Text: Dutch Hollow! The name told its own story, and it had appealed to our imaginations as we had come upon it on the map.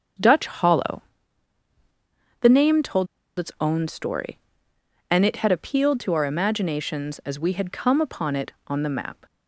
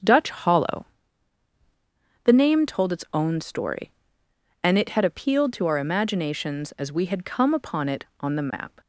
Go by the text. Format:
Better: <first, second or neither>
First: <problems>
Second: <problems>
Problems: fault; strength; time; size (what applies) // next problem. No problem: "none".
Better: second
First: starts louder than the rest; strong; until 2.5 s; 7 dB // pauses between "told" and "its"; slight; at 3.0 s; 0.30 s long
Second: starts louder than the rest; strong; until 2.3 s; 7 dB